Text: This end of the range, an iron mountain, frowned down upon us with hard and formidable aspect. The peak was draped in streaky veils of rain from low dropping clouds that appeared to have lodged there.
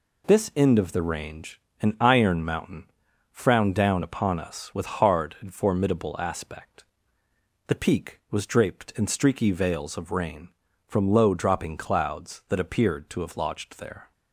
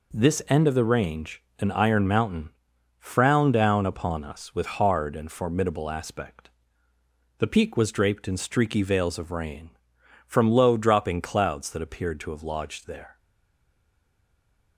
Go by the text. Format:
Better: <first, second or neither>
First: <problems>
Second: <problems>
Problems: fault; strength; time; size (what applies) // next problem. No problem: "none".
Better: first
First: none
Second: stays silent after the last word; noticeable; from 13.1 s on; 1.6 s long